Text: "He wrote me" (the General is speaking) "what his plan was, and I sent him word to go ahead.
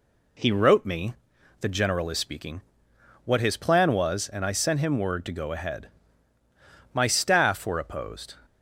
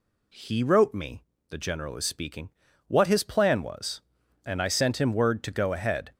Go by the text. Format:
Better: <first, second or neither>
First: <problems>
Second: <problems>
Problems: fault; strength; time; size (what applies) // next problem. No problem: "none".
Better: second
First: goes on to say "My staff were opposed"; from 6.9 s on; 1.4 s long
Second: none